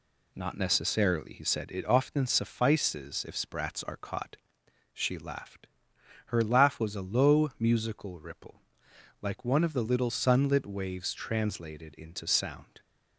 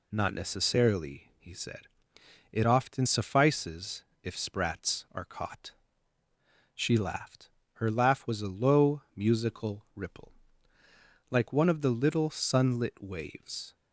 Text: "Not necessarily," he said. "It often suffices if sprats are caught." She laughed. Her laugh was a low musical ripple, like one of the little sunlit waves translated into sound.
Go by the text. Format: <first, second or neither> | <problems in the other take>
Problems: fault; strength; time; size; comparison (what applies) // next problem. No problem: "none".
first | pauses between "suffices" and "if"; slight; at 4.0 s; 0.20 s long // stops before "translated into sound"; at 13.7 s